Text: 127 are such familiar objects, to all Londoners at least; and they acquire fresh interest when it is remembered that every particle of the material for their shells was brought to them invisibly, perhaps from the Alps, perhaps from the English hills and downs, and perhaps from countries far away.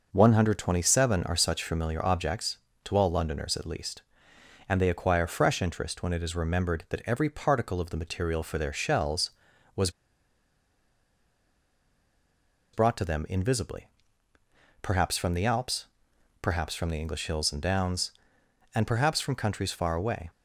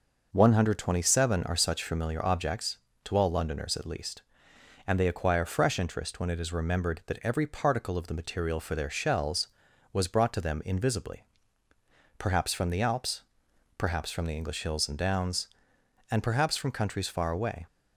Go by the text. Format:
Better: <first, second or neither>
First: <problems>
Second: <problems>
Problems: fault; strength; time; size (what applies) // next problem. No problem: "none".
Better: second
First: pauses between "was" and "brought"; strong; at 9.8 s; 2.8 s long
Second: none